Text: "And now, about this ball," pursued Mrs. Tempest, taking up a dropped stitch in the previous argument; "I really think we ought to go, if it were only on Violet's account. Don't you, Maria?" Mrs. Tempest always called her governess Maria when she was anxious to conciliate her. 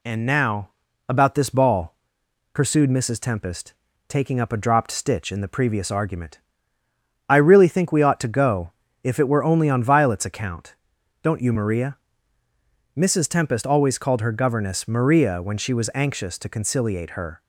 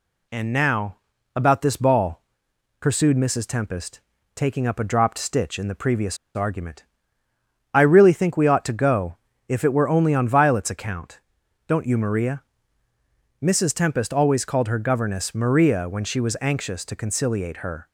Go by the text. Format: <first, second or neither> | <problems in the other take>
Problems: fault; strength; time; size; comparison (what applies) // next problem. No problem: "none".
first | pauses between "previous" and "argument"; slight; at 6.1 s; 0.19 s long